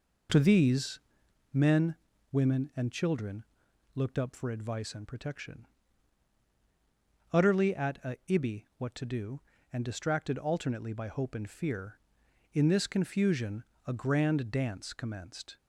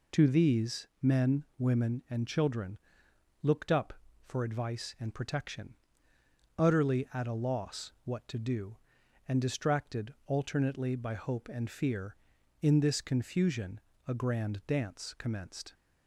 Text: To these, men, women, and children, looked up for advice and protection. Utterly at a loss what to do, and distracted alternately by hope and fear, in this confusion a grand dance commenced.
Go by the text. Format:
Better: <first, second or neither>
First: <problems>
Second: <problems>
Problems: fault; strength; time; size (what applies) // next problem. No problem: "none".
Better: second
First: says "ibi" for "loss"; at 8.2 s // pauses between "confusion" and "a"; slight; at 13.6 s; 0.20 s long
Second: pauses between "confusion" and "a"; slight; at 13.7 s; 0.28 s long